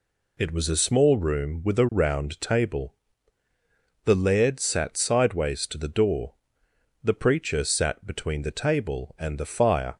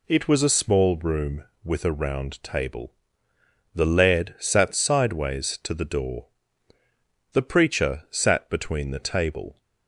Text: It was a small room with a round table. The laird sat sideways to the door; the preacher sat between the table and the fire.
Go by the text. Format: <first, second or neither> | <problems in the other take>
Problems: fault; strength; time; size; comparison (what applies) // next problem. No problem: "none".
first | stops before "and the fire"; at 9.6 s